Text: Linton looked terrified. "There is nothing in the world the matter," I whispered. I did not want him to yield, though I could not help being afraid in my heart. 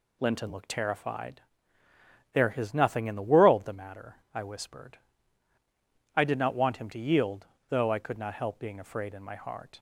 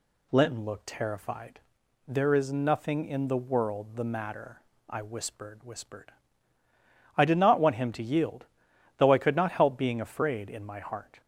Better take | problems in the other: first | says "whispered" twice; at 5.6 s

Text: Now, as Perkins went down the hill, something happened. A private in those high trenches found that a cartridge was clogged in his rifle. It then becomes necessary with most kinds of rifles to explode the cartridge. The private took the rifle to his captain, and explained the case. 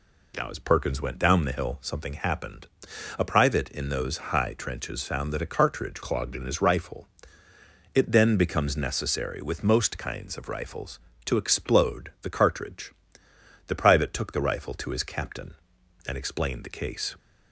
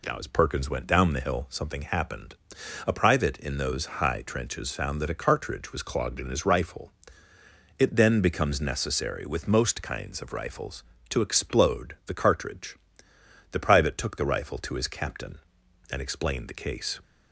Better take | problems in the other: second | skips "was"; at 6.0 s

